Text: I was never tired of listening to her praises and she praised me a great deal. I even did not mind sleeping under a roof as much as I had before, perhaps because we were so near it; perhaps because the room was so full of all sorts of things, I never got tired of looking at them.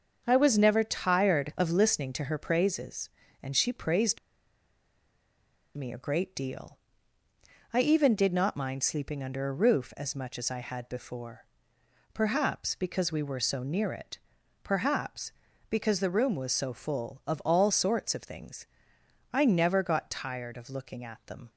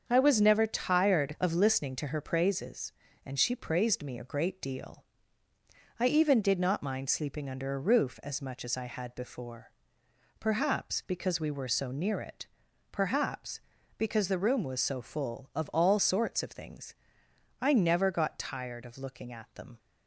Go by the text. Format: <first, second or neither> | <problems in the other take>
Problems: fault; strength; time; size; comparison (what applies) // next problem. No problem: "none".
second | starts louder than the rest; until 1.2 s; 6.5 dB; also in the second // pauses between "praised" and "me"; strong; at 4.1 s; 1.5 s long